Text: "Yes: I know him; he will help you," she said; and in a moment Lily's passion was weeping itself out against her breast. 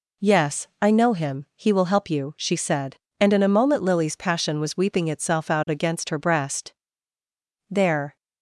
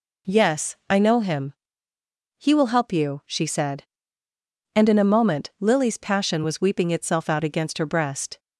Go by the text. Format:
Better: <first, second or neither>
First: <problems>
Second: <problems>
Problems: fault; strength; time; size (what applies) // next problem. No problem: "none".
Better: second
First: goes on to say "There"; slight; from 7.6 s on; 0.46 s long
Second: none